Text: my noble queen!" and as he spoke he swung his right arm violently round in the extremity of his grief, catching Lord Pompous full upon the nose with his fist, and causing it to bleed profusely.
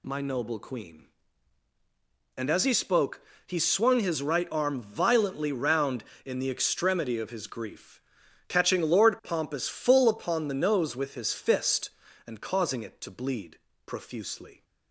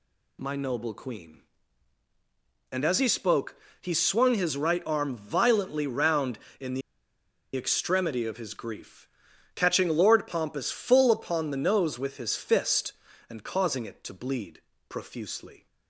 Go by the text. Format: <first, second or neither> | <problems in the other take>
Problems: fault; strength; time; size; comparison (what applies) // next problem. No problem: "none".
first | pauses between "spoke" and "he"; slight; at 3.5 s; 0.26 s long; slight in the first // pauses between "the" and "extremity"; noticeable; at 6.8 s; 0.75 s long // pauses between "bleed" and "profusely"; slight; at 14.6 s; 0.28 s long; slight in the first